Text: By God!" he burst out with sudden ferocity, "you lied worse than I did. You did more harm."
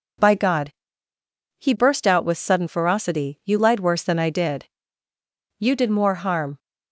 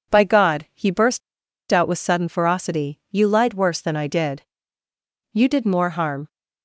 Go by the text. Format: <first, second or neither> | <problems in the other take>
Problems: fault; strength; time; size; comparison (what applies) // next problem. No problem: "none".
first | pauses between "burst" and "out"; noticeable; at 1.2 s; 0.51 s long